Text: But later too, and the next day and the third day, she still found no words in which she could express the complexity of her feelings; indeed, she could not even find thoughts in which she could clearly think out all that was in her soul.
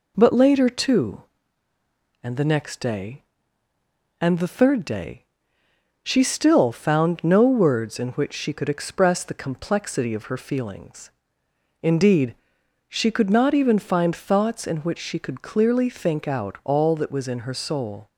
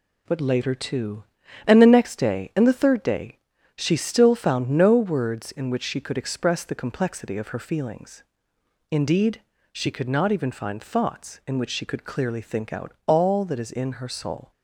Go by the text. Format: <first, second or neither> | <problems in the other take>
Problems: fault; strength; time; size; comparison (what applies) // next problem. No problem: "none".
first | pauses between "out" and "all"; slight; at 12.9 s; 0.16 s long // says "is" for "was"; at 13.6 s